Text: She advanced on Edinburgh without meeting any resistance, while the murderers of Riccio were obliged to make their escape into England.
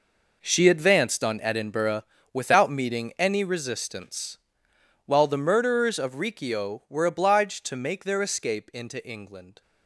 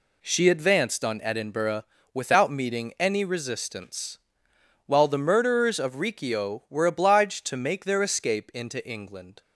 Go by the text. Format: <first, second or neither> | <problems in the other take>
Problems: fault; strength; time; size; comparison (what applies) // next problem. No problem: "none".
second | gets quieter; strong; throughout; 13 dB // pauses between "Edinburgh" and "without"; slight; at 2.0 s; 0.30 s long; slight in the second